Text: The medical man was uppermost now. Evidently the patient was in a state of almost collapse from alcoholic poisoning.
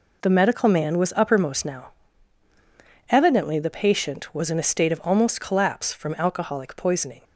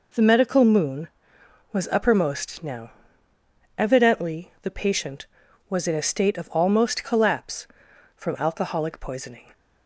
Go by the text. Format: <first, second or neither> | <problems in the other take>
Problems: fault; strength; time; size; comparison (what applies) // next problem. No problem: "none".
first | says "moon" for "man"; at 0.6 s